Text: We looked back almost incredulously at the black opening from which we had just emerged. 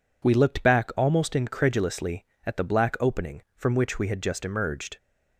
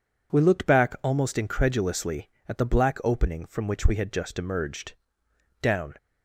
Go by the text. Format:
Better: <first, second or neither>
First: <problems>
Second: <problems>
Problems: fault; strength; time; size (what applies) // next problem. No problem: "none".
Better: first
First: none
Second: goes on to say "Down"; slight; from 5.6 s on; 0.34 s long